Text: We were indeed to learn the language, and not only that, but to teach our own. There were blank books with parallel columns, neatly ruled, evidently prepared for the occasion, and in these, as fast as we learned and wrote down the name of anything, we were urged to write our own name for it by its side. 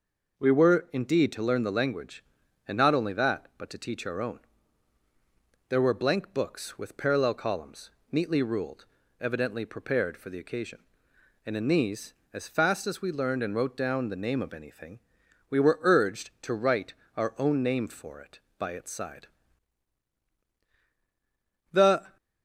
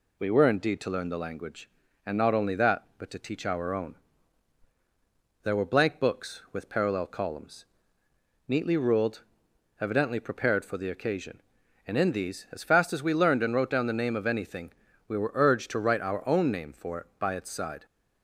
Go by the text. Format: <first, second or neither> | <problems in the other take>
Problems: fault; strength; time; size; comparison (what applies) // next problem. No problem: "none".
second | pauses between "write" and "our"; slight; at 16.9 s; 0.24 s long // goes on to say "The"; slight; from 21.7 s on; 0.44 s long